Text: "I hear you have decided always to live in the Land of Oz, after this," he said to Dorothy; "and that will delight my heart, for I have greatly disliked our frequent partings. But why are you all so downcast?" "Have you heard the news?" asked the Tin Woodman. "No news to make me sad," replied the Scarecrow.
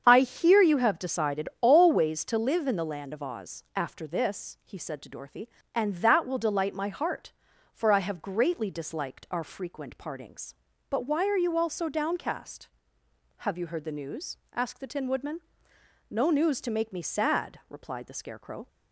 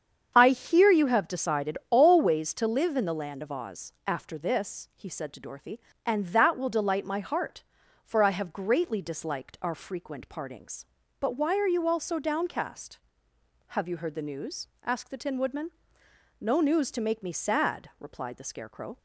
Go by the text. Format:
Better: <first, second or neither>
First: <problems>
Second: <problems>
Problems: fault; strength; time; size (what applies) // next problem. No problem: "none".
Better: neither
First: starts louder than the rest; strong; until 1.0 s; 7.5 dB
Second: starts louder than the rest; strong; until 1.3 s; 7.5 dB